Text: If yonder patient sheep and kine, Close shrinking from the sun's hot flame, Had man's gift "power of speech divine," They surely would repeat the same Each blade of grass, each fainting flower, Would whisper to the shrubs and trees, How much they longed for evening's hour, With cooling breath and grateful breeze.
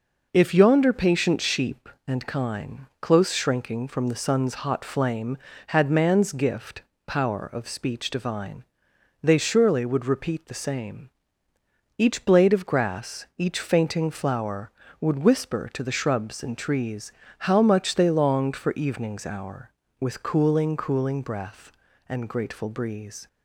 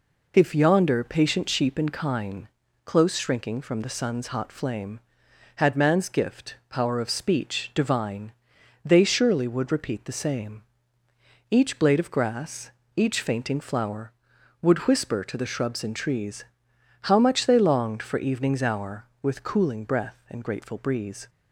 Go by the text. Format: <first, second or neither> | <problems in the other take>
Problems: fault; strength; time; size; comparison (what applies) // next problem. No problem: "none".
second | pauses between "gift" and "power"; slight; at 6.8 s; 0.24 s long // pauses between "same" and "Each"; noticeable; at 11.0 s; 0.88 s long; noticeable in the second // says "cooling" twice; at 20.7 s